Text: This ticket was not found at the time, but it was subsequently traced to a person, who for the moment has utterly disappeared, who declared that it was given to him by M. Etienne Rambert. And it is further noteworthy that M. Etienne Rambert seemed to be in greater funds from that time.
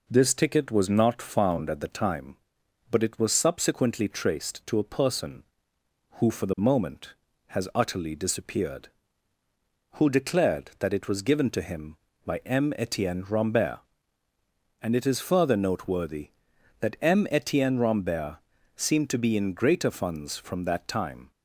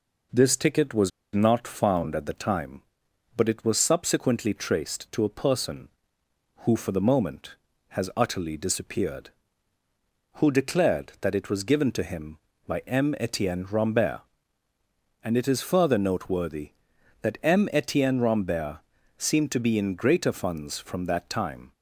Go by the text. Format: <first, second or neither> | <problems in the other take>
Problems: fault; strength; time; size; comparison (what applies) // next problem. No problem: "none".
first | pauses between "was" and "not"; slight; at 1.1 s; 0.24 s long // pauses between "Rambert" and "seemed"; at 18.7 s; 0.38 s long; also in the first